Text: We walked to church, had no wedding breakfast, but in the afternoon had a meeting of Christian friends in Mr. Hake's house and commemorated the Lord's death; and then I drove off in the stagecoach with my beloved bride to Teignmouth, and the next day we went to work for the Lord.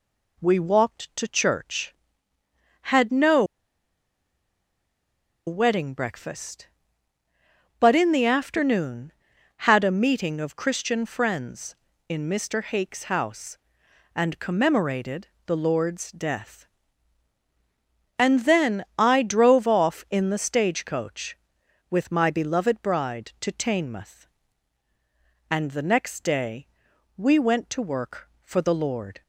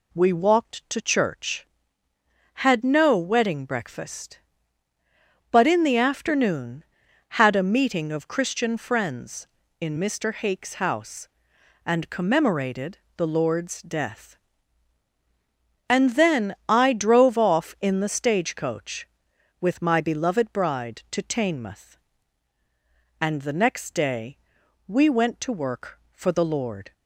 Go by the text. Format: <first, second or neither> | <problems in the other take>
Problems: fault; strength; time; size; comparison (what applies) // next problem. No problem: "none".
second | pauses between "no" and "wedding"; strong; at 3.4 s; 2.0 s long // pauses between "commemorated" and "the"; slight; at 15.2 s; 0.20 s long; slight in the second // pauses between "day" and "we"; noticeable; at 26.6 s; 0.48 s long; noticeable in the second